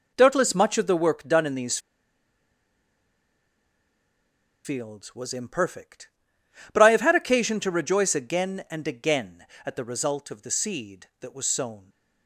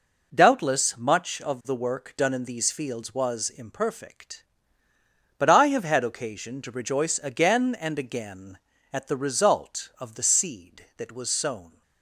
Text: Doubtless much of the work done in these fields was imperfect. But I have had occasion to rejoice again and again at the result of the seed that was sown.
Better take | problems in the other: second | pauses between "these" and "fields"; strong; at 1.7 s; 2.8 s long

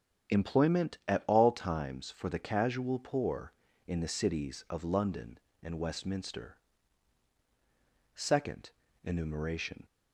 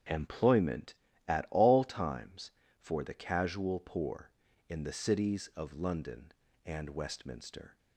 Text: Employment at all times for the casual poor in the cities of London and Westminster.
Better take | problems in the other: second | starts louder than the rest; strong; until 1.4 s; 8.5 dB; strong in the second // goes on to say "Second Enumeration"; strong; from 8.1 s on; 1.7 s long

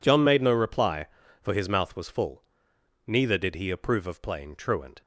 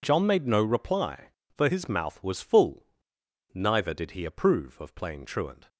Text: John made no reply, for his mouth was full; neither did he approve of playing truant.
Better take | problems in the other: neither | none

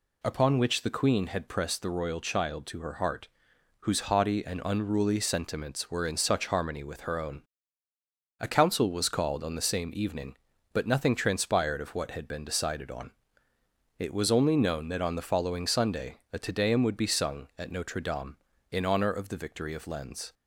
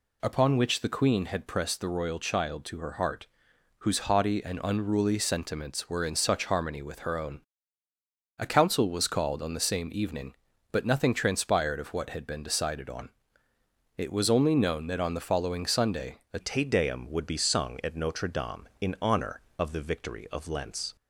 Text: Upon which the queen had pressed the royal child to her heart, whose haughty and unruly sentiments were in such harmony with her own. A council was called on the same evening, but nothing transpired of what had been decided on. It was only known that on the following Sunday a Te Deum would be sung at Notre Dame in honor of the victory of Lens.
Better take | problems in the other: first | changes voice at "Te"; from 16.4 s on; 4.5 s long

